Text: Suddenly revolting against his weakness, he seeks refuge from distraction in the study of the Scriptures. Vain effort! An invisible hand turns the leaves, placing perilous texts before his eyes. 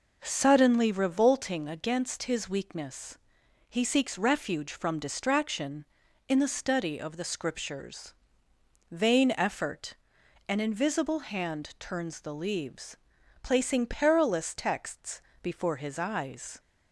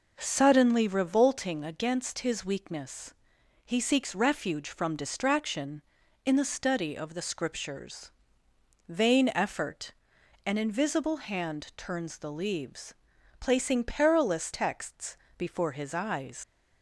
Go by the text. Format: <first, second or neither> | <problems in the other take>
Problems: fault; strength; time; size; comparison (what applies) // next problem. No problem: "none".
first | pauses between "texts" and "before"; slight; at 15.1 s; 0.20 s long; slight in the first // leaves "eyes" unfinished; at 16.4 s; 110 ms